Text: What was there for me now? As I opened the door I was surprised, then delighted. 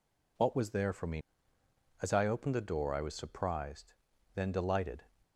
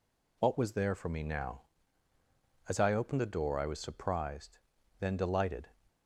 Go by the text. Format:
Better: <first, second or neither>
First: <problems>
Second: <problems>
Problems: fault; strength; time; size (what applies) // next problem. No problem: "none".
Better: second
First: skips "now"; at 1.6 s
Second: none